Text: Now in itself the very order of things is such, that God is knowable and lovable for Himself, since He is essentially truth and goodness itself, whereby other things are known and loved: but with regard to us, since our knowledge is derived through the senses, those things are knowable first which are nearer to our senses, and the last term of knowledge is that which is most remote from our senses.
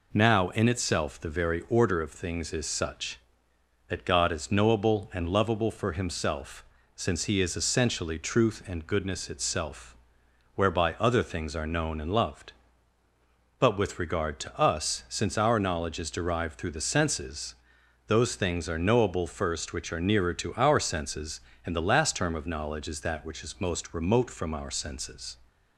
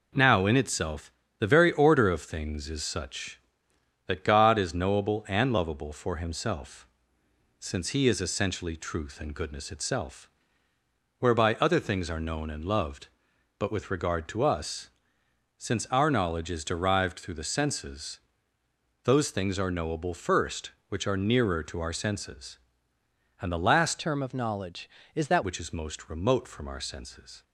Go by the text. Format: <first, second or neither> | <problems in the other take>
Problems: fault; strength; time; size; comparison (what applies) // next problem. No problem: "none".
first | pauses between "itself" and "the"; slight; at 1.1 s; 0.28 s long // changes voice from "term" to "that"; from 23.9 to 25.4 s; 1.5 s long